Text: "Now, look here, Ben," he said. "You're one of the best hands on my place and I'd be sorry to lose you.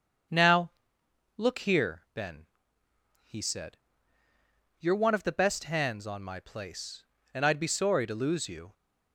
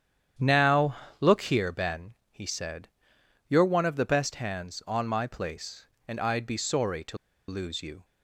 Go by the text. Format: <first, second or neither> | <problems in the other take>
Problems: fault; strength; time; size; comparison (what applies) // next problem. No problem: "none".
first | starts louder than the rest; strong; until 1.6 s; 9 dB; strong in the first // pauses between "to" and "lose"; slight; at 7.1 s; 0.31 s long